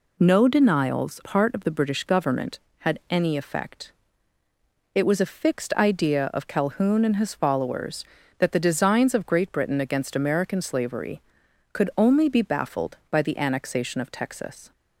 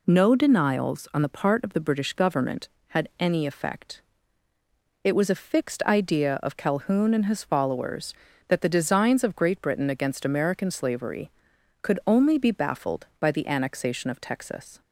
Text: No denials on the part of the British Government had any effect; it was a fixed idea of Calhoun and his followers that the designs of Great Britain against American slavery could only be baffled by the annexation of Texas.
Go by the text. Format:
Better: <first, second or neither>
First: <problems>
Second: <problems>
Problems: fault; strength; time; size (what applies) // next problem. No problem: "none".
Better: second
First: skips "on the"; at 1.2 s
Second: none